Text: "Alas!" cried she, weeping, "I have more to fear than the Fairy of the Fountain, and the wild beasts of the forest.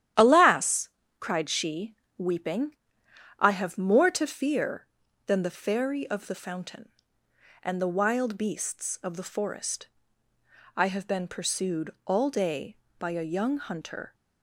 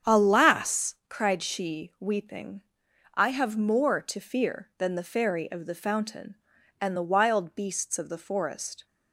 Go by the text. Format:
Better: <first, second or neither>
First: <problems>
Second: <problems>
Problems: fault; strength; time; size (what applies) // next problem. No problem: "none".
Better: second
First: starts louder than the rest; strong; until 1.4 s; 11 dB // goes on to say "I have been pursued all day by a young hunter"; strong; from 10.7 s on; 3.3 s long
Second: starts louder than the rest; strong; until 1.2 s; 8 dB